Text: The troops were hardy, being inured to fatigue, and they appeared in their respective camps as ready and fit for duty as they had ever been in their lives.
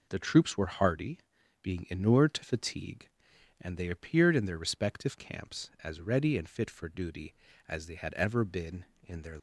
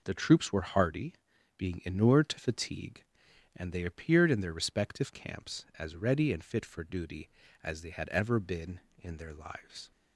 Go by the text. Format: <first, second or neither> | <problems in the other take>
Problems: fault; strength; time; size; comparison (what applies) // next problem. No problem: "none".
second | stops before "lives"; at 9.3 s